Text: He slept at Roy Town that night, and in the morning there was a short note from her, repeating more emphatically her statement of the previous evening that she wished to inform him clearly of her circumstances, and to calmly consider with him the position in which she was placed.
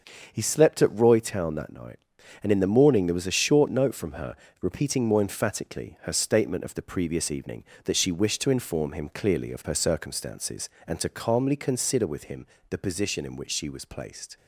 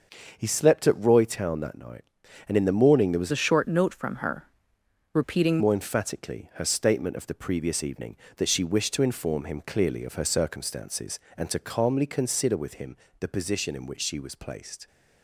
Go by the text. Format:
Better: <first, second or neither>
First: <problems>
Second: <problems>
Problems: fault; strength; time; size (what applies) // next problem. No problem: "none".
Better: first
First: starts louder than the rest; until 1.3 s; 6.5 dB // pauses between "him" and "the"; slight; at 12.4 s; 0.24 s long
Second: starts louder than the rest; until 1.3 s; 6.5 dB // changes voice from "a" to "repeating"; from 3.3 to 5.5 s; 2.2 s long // pauses between "him" and "the"; slight; at 12.9 s; 0.24 s long